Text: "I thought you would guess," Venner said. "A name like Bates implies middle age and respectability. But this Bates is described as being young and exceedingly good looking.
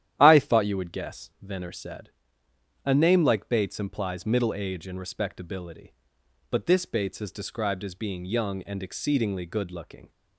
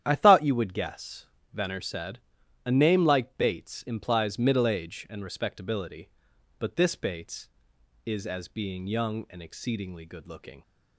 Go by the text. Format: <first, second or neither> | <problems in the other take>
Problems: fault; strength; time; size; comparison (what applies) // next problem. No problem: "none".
first | starts louder than the rest; strong; until 1.0 s; 10.5 dB; strong in the first // skips "described"; at 8.2 s